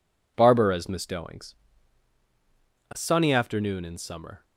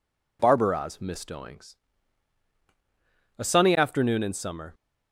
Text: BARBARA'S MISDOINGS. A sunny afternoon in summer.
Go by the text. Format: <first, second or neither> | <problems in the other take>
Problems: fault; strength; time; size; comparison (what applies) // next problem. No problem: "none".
neither | none